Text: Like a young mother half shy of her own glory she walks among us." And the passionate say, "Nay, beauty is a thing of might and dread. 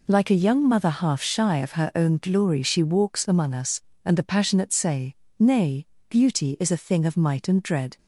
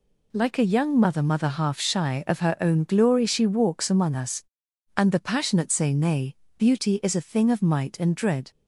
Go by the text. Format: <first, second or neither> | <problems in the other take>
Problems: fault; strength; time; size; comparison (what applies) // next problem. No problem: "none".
first | says "mother" twice; at 1.2 s